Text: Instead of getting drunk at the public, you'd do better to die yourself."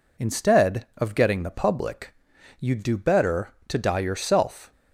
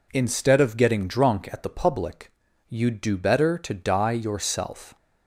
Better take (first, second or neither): second